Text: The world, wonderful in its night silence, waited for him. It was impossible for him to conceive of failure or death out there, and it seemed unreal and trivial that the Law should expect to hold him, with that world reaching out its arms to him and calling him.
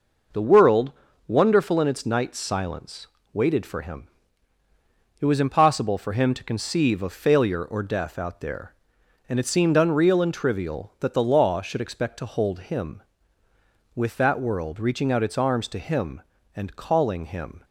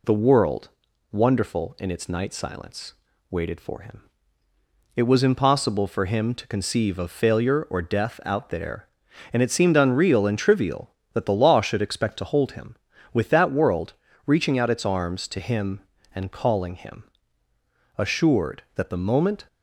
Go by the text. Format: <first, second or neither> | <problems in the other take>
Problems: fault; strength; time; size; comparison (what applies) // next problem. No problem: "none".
first | pauses between "world" and "reaching"; slight; at 13.9 s; 0.34 s long // goes on to say "Assured that the moment"; from 17.9 s on; 1.5 s long